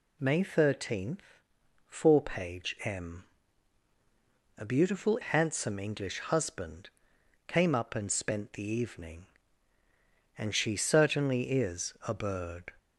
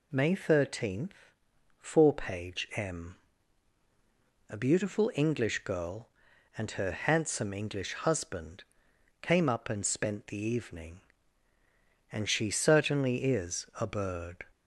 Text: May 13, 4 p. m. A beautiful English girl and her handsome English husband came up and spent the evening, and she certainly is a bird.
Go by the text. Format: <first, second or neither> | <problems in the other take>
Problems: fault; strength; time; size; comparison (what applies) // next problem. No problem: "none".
second | skips "English girl and her"; at 5.1 s // pauses between "husband" and "came"; noticeable; at 6.8 s; 0.58 s long; noticeable in the second // pauses between "is" and "a"; slight; at 11.9 s; 0.16 s long; slight in the second